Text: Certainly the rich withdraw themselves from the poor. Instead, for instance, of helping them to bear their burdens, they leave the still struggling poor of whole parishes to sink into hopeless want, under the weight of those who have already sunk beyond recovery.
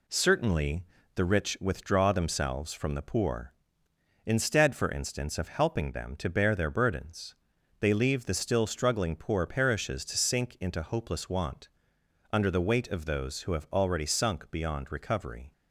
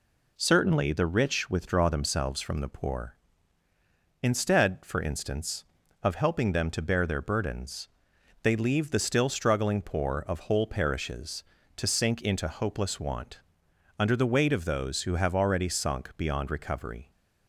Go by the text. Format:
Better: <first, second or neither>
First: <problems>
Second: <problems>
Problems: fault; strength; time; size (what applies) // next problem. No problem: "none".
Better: second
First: pauses between "Certainly" and "the"; slight; at 0.8 s; 0.32 s long // skips "of whole"; at 9.4 s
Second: none